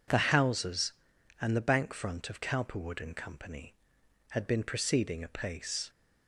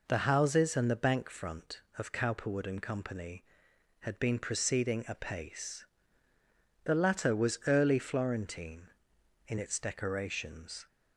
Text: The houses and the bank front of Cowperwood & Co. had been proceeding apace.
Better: first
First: none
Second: goes on to say "The latter was early Florentine in its decorations"; strong; from 6.8 s on; 4.0 s long

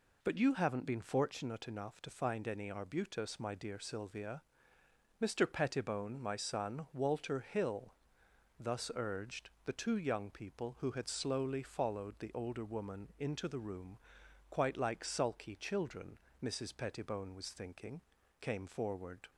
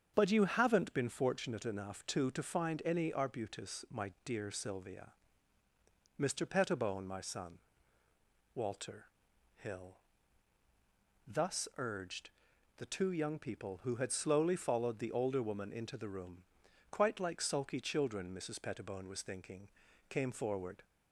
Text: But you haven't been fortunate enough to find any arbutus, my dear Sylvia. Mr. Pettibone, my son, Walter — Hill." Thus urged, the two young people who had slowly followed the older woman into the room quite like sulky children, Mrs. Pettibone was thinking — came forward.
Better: first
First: pauses between "room" and "quite"; noticeable; at 13.9 s; 0.54 s long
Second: starts louder than the rest; strong; until 1.1 s; 7.5 dB // says "to" twice; at 2.3 s // pauses between "room" and "quite"; noticeable; at 16.4 s; 0.48 s long

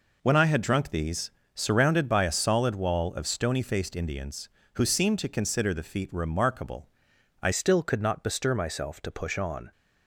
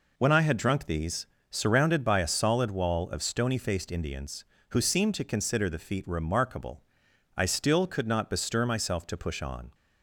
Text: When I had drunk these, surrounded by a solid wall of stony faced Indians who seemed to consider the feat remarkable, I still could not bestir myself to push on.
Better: second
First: changes voice at "still"; from 7.5 s on; 2.2 s long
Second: none

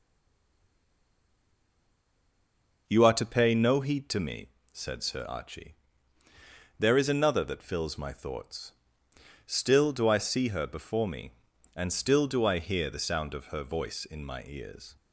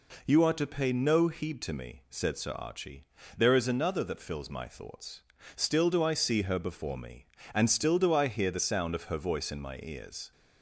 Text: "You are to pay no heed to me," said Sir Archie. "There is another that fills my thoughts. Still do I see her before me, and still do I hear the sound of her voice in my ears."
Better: second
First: stays silent before the first word; strong; until 2.8 s; 2.8 s long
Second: none

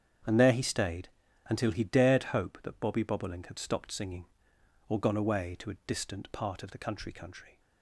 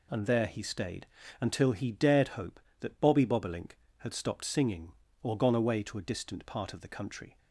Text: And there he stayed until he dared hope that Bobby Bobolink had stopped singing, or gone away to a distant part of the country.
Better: second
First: starts louder than the rest; strong; until 1.6 s; 8 dB // pauses between "stayed" and "until"; slight; at 1.0 s; 0.36 s long // says "country" twice; at 7.1 s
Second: pauses between "stayed" and "until"; slight; at 1.0 s; 0.34 s long

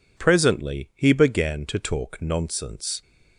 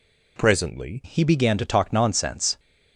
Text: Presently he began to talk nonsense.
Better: first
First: none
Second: changes voice at "he"; from 1.0 s on; 1.5 s long

